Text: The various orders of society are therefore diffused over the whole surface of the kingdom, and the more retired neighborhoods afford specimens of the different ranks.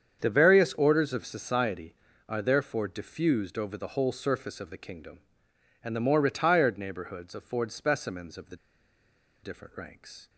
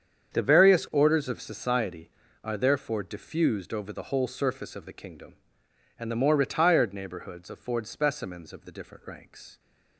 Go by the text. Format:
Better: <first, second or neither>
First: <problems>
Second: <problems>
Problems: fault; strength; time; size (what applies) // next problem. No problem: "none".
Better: second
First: starts louder than the rest; strong; until 1.2 s; 7.5 dB // pauses between "the" and "different"; noticeable; at 8.5 s; 0.86 s long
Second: starts louder than the rest; strong; until 1.3 s; 7.5 dB